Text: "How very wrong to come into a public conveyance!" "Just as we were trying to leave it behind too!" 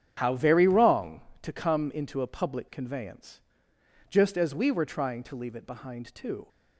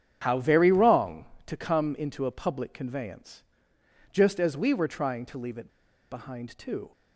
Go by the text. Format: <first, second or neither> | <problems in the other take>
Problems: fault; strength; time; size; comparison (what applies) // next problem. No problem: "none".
first | starts louder than the rest; strong; until 1.2 s; 8.5 dB; strong in the first // pauses between "it" and "behind"; at 5.6 s; 0.42 s long